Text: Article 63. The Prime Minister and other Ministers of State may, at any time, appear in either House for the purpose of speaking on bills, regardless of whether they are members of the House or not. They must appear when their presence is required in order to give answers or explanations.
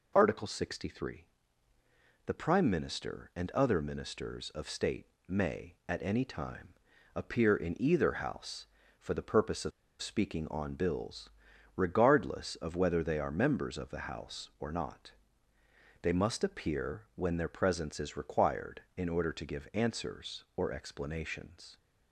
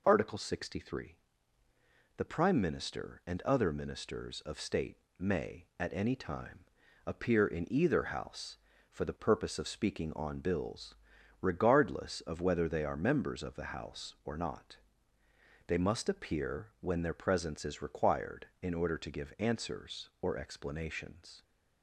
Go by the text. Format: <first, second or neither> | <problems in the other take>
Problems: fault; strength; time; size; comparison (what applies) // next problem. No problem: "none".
second | pauses between "State" and "may"; slight; at 5.0 s; 0.20 s long; slight in the second // pauses between "of" and "speaking"; slight; at 9.7 s; 0.30 s long